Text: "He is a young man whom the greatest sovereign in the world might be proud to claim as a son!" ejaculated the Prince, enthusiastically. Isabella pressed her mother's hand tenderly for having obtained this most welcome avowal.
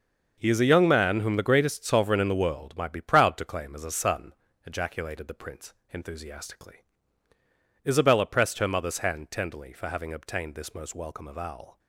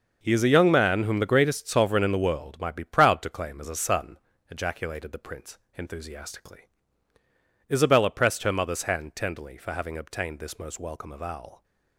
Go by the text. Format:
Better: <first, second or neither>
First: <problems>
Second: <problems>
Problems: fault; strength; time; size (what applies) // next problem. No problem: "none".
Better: neither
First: starts louder than the rest; noticeable; until 1.3 s; 6 dB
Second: starts louder than the rest; noticeable; until 1.2 s; 6 dB